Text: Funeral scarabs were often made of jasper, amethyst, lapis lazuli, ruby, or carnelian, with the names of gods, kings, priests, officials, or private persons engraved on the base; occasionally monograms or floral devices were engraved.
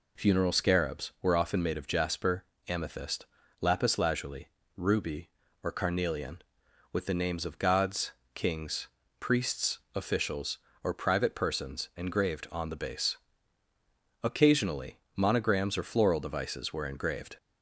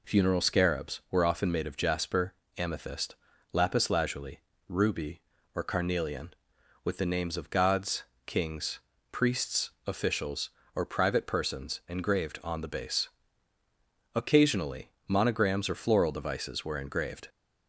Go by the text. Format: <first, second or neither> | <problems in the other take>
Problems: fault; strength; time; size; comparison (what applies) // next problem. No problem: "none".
neither | pauses between "occasionally" and "monograms"; slight; the same in both